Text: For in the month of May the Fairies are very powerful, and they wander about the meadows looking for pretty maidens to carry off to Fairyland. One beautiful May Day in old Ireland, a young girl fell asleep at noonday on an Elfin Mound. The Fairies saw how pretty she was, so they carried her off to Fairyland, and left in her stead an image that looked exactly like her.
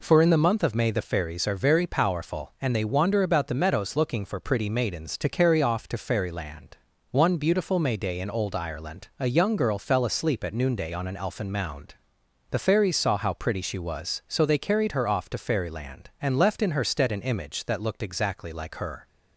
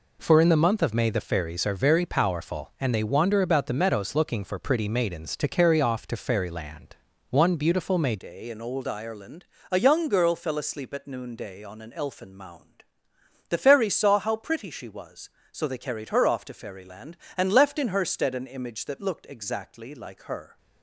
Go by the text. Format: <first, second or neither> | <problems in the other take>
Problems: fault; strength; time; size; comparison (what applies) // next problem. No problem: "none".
first | changes voice at "Day"; from 8.1 s on; 12.4 s long